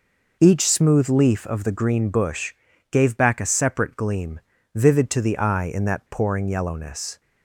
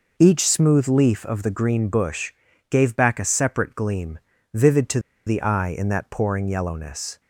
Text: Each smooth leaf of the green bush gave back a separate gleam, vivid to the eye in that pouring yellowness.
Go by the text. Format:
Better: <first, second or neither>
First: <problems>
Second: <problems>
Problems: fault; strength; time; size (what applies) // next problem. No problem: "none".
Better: first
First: pauses between "bush" and "gave"; at 2.5 s; 0.40 s long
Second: pauses between "bush" and "gave"; at 2.3 s; 0.40 s long // pauses between "to" and "the"; slight; at 5.0 s; 0.25 s long